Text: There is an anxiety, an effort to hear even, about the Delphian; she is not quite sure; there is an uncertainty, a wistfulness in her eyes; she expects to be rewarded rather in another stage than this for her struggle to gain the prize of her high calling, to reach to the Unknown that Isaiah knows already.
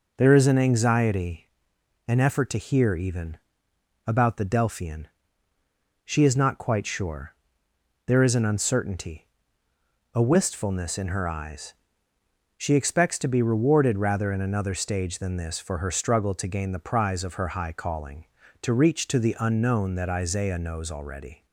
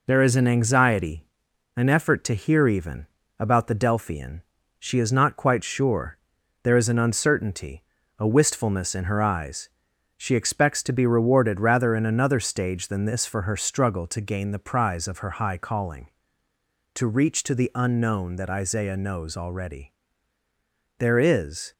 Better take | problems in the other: first | goes on to say "There is"; noticeable; from 20.9 s on; 0.74 s long

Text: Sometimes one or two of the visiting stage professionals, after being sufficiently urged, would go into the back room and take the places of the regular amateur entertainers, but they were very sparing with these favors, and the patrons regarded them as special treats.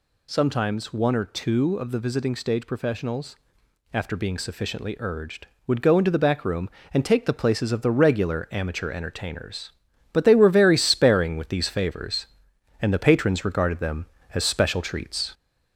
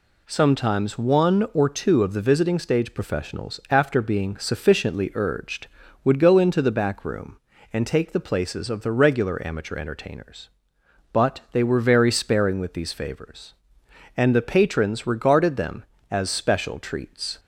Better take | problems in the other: second | gets louder; slight; throughout; 3 dB

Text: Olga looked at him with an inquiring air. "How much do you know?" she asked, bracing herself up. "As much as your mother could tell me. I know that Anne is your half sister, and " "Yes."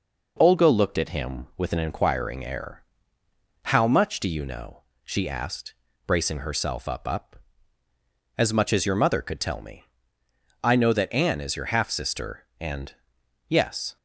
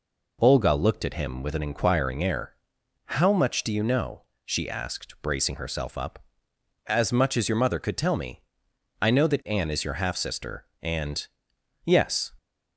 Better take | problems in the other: second | says "up" twice; at 7.0 s

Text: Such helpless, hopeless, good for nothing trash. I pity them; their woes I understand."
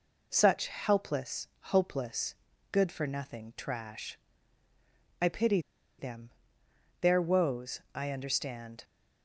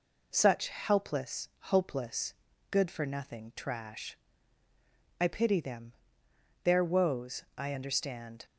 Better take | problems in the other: second | pauses between "pity" and "them"; at 5.5 s; 0.39 s long // pauses between "woes" and "I"; slight; at 7.7 s; 0.16 s long; slight in the second

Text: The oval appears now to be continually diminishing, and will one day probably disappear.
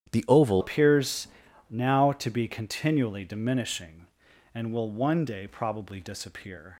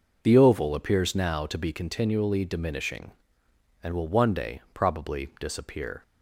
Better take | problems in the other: second | starts louder than the rest; strong; until 1.1 s; 10 dB // changes voice at "appears"; from 0.5 s on; 6.2 s long // pauses between "appears" and "now"; at 1.2 s; 0.44 s long

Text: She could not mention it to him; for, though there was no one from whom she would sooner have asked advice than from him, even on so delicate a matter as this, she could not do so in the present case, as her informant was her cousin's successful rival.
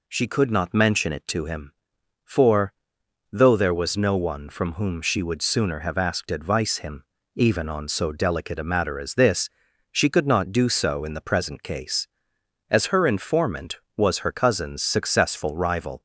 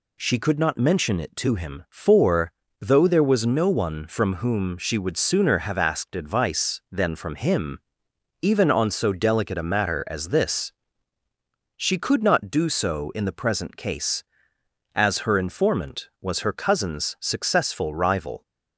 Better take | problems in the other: second | skips "than from"; at 6.7 s

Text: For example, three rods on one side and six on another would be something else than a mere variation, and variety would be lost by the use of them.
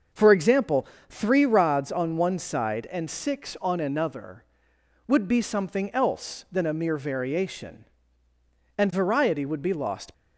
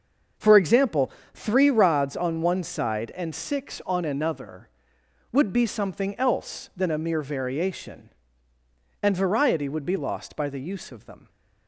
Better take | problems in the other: second | starts louder than the rest; until 1.3 s; 6 dB; also in the second // stops before "by the use of them"; at 10.1 s

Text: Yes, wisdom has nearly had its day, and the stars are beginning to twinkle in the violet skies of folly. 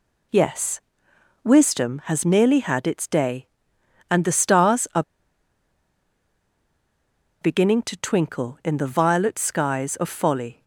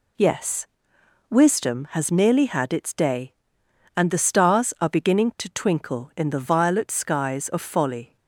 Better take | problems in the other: second | pauses between "are" and "beginning"; strong; at 5.0 s; 2.4 s long

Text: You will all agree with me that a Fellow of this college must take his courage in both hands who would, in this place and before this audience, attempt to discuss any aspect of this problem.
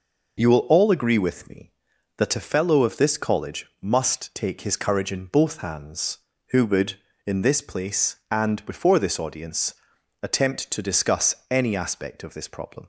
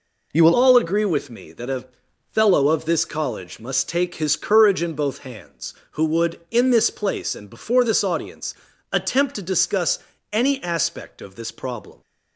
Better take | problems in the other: first | changes voice at "all"; from 0.5 s on; 11.5 s long // pauses between "a" and "Fellow"; noticeable; at 1.8 s; 0.48 s long // pauses between "discuss" and "any"; slight; at 9.9 s; 0.34 s long; slight in the first

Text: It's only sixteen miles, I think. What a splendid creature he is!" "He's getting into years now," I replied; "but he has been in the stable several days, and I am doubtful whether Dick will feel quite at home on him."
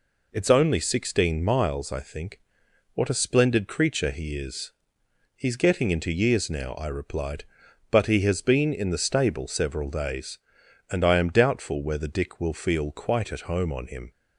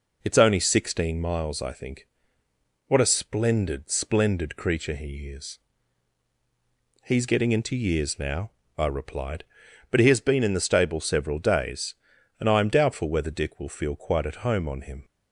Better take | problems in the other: first | says "splendid" twice; at 3.8 s

